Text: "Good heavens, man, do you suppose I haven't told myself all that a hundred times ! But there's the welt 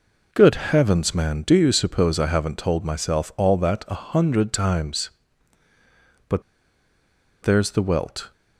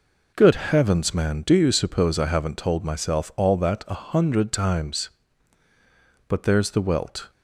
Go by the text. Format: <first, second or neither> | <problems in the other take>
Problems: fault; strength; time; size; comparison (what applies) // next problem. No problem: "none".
second | pauses between "But" and "there's"; at 6.4 s; 1.0 s long